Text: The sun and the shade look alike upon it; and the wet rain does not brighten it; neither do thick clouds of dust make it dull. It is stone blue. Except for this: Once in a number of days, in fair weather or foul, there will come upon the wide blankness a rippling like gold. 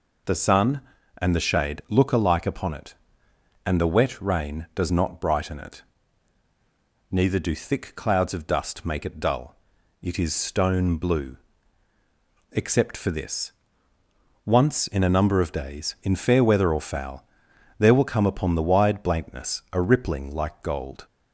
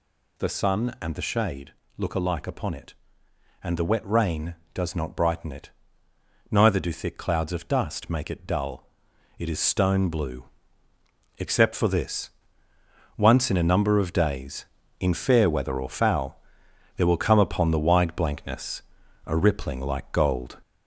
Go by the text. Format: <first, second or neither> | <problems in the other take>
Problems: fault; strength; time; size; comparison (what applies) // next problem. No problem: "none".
first | gets louder; noticeable; throughout; 4.5 dB // pauses between "shade" and "look"; slight; at 1.7 s; 0.22 s long // pauses between "blankness" and "a"; at 18.8 s; 0.44 s long